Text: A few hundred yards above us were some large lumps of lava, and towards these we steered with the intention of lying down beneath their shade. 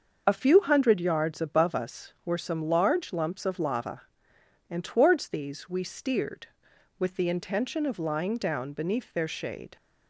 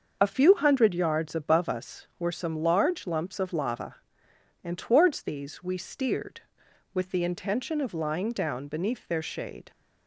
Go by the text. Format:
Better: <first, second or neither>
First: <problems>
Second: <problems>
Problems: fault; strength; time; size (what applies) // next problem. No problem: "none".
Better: neither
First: starts louder than the rest; until 1.2 s; 6.5 dB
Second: starts louder than the rest; until 1.2 s; 6.5 dB